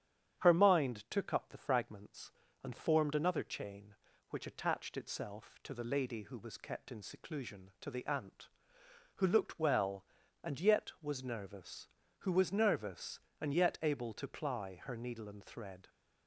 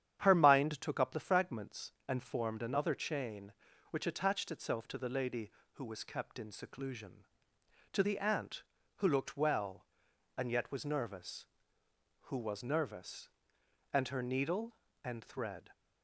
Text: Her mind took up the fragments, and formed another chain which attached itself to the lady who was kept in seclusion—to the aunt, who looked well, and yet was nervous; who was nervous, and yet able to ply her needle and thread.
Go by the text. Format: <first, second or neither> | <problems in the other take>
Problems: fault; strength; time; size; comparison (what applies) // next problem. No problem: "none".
first | starts louder than the rest; strong; until 1.2 s; 9.5 dB; strong in the first // skips "yet able to ply"; at 14.0 s